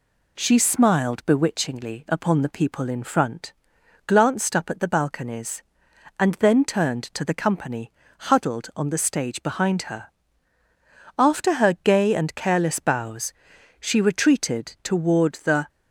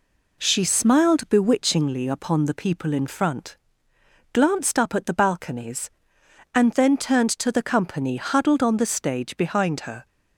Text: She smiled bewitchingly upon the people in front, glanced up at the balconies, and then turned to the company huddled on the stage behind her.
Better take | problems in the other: second | pauses between "company" and "huddled"; slight; at 7.9 s; 0.28 s long // goes on to say "After her gay and careless bows she retreated toward the"; strong; from 11.1 s on; 4.5 s long

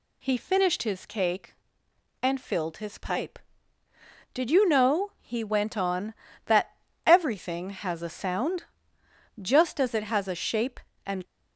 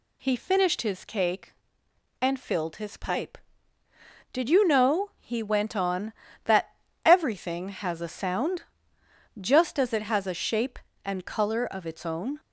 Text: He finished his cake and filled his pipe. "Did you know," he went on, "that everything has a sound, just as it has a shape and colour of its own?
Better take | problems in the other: second | pauses between "that" and "everything"; slight; at 6.7 s; 0.30 s long; slight in the second // stops before "colour of its own"; at 11.2 s

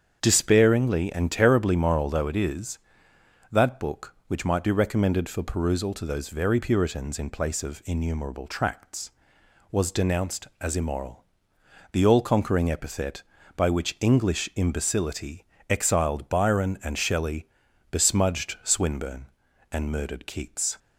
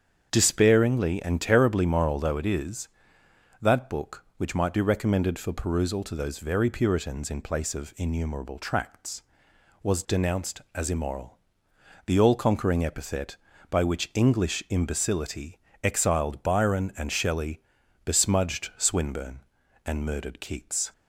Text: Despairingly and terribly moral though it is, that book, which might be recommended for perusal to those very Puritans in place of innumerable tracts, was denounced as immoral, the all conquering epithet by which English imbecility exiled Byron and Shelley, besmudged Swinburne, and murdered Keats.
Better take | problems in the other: neither | starts louder than the rest; strong; the same in both // pauses between "imbecility" and "exiled"; slight; the same in both

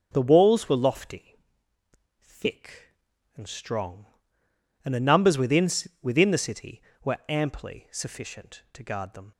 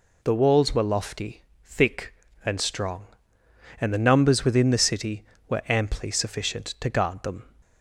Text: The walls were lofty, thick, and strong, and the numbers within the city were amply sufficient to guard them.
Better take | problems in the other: second | starts louder than the rest; until 1.1 s; 7 dB // says "within" twice; at 6.0 s

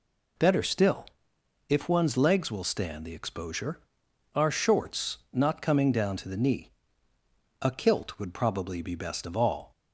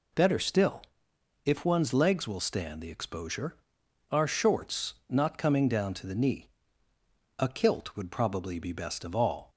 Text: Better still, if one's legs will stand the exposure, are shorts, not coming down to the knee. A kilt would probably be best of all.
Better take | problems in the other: neither | none

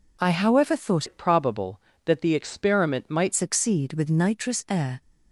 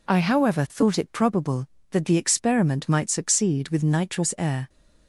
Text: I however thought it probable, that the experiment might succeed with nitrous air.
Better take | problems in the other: second | changes voice from "it" to "might"; from 1.0 to 3.3 s; 2.3 s long

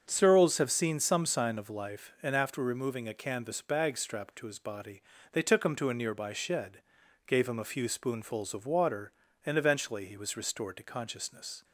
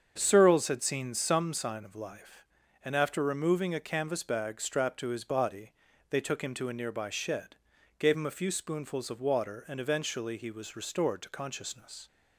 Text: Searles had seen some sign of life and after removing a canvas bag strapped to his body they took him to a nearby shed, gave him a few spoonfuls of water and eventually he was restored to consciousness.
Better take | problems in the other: second | starts louder than the rest; until 1.0 s; 6.5 dB; also in the second // says "have" for "had"; at 0.5 s // pauses between "body" and "they"; slight; at 5.0 s; 0.30 s long; slight in the second

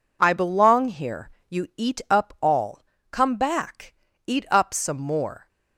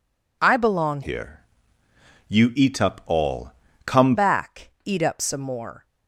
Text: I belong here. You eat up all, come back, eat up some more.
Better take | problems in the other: first | changes voice from "here" to "come"; from 1.0 to 4.1 s; 3.1 s long

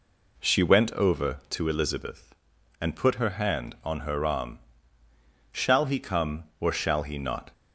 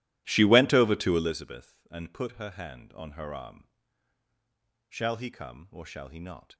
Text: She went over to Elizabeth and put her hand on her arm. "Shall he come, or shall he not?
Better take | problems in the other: first | starts louder than the rest; strong; until 1.4 s; 14.5 dB

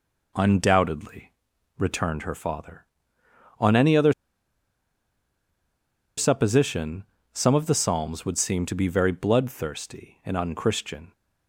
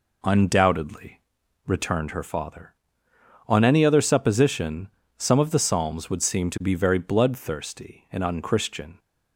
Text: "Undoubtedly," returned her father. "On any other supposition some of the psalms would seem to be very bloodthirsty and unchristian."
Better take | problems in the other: second | pauses between "other" and "supposition"; strong; at 4.1 s; 2.0 s long // pauses between "supposition" and "some"; slight; at 7.0 s; 0.28 s long; slight in the second

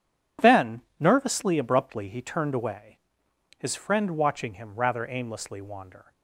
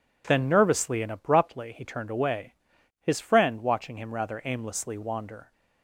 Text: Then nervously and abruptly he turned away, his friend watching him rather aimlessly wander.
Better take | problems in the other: second | pauses between "Then" and "nervously"; slight; at 0.8 s; 0.16 s long // skips "and"; at 1.5 s

